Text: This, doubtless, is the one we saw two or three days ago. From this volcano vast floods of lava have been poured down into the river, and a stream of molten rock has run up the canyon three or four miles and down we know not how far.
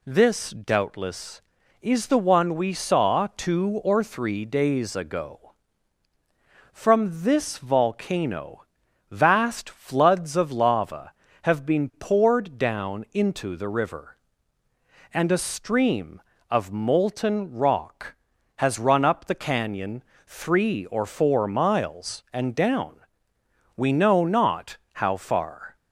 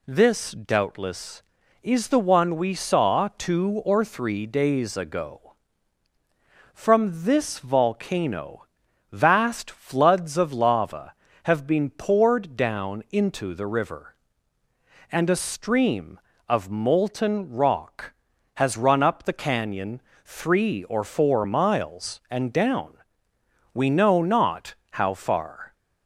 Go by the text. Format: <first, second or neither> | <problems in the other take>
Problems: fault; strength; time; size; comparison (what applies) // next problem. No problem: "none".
neither | pauses between "volcano" and "vast"; noticeable; the same in both // pauses between "canyon" and "three"; slight; the same in both // pauses between "down" and "we"; noticeable; the same in both // pauses between "not" and "how"; slight; the same in both